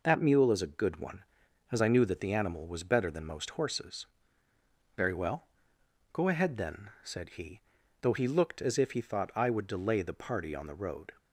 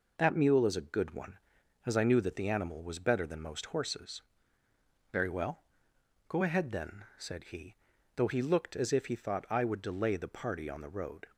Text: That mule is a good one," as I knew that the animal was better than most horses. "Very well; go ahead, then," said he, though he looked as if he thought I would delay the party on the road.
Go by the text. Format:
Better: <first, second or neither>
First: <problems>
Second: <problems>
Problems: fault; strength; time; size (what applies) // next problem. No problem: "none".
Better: neither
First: none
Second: none